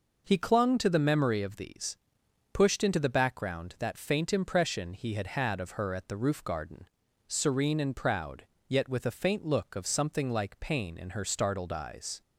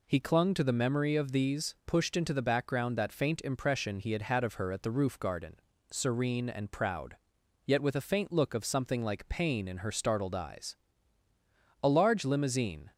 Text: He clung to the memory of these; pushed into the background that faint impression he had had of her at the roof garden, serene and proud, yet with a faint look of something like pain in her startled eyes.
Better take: first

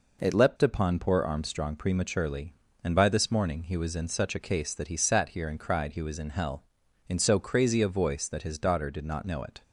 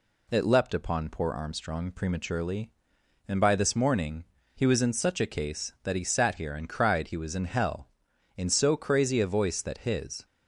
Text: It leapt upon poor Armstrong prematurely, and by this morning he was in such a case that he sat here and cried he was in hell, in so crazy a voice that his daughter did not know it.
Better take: first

